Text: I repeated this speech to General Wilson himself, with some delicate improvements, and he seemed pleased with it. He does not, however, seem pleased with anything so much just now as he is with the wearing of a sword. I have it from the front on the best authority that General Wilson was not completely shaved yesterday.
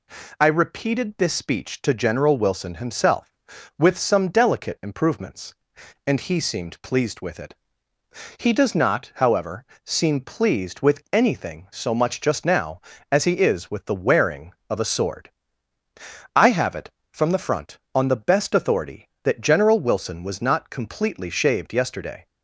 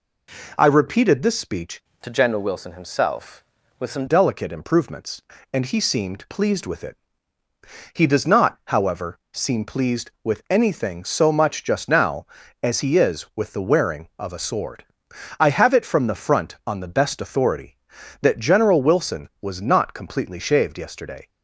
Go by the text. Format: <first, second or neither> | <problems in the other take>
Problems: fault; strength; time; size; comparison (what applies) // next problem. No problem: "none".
first | changes voice from "to" to "some"; from 2.0 to 4.0 s; 2.0 s long